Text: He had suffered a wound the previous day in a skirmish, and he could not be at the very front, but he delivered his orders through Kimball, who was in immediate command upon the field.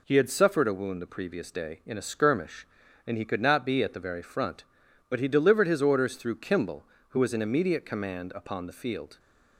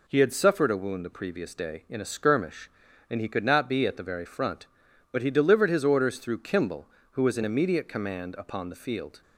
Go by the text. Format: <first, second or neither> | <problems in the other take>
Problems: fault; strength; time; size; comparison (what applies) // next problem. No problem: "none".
neither | none